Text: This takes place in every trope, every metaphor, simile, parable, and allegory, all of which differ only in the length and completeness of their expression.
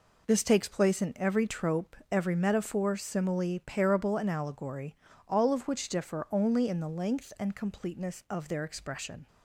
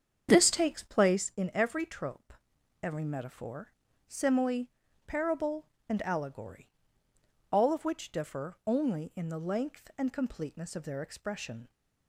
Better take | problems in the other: first | starts louder than the rest; strong; until 1.3 s; 7.5 dB

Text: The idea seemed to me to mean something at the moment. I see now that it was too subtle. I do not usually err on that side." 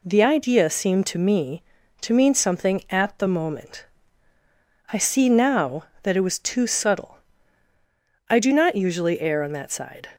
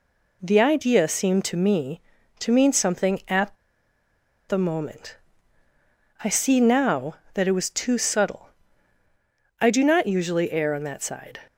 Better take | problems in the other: first | pauses between "at" and "the"; noticeable; at 3.5 s; 0.93 s long

